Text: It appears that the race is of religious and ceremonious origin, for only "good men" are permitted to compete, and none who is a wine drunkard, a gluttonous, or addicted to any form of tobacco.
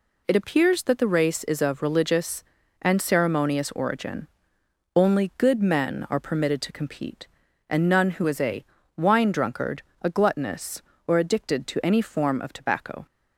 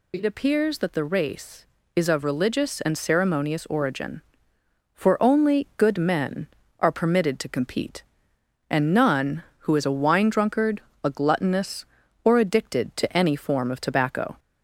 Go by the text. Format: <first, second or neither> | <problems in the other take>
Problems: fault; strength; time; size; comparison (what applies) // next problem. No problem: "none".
second | skips "for"; at 4.6 s // pauses between "a" and "wine"; slight; at 8.6 s; 0.32 s long